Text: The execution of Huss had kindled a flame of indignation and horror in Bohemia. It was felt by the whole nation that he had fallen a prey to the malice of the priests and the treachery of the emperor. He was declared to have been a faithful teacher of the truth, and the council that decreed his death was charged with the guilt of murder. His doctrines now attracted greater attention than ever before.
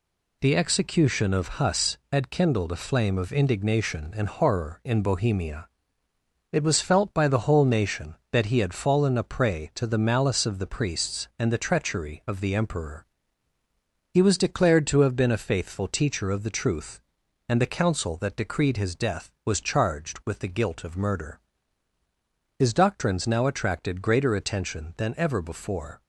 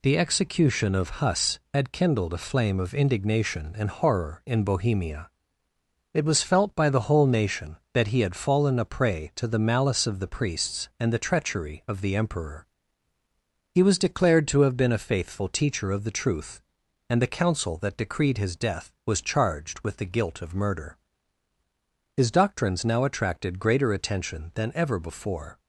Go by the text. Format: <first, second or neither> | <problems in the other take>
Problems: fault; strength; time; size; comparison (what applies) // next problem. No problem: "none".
neither | none